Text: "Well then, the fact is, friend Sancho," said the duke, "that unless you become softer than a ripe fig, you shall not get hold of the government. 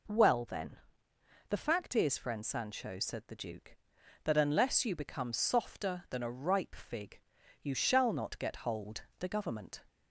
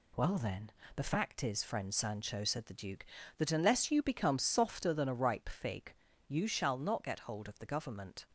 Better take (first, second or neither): second